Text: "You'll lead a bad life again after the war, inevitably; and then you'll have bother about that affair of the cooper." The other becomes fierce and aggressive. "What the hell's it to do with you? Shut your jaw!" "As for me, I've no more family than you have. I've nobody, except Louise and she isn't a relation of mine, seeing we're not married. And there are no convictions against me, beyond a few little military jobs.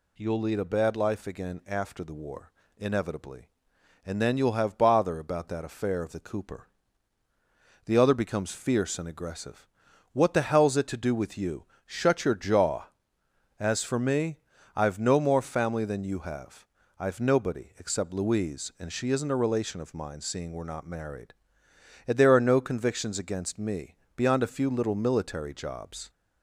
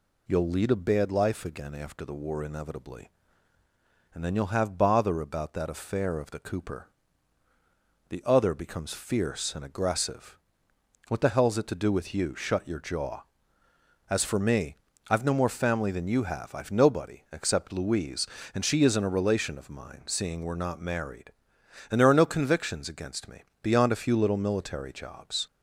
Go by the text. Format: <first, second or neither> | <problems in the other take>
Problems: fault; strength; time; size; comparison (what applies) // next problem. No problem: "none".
neither | none